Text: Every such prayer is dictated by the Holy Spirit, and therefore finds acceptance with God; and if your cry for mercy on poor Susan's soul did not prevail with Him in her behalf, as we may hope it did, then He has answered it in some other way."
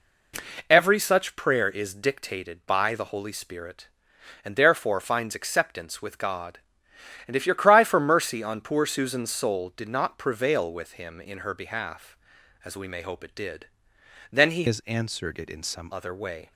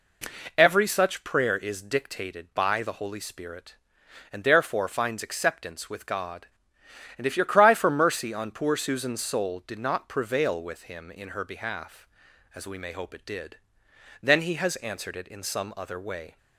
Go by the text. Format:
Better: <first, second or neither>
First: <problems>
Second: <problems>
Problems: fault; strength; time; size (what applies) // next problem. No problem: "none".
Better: second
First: changes voice from "has" to "some"; from 14.6 to 15.9 s; 1.3 s long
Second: none